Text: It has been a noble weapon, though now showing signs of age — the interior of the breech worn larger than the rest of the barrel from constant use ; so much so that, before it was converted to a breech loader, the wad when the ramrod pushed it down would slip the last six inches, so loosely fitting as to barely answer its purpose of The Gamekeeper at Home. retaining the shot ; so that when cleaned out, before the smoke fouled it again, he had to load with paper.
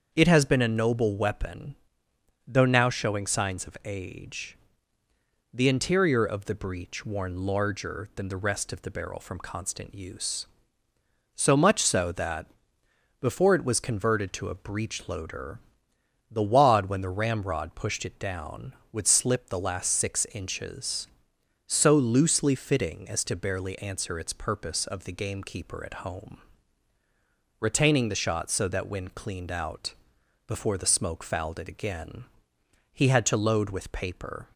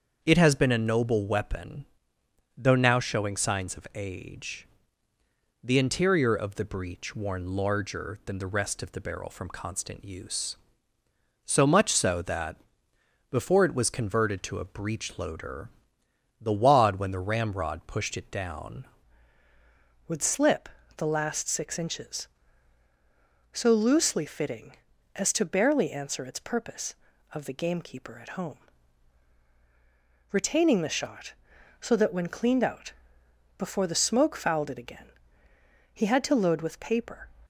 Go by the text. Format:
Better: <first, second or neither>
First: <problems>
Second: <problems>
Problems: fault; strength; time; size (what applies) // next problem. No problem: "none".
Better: first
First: starts louder than the rest; until 1.1 s; 7 dB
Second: starts louder than the rest; until 1.2 s; 7 dB // changes voice at "would"; from 20.0 s on; 17.2 s long // pauses between "slip" and "the"; slight; at 20.6 s; 0.28 s long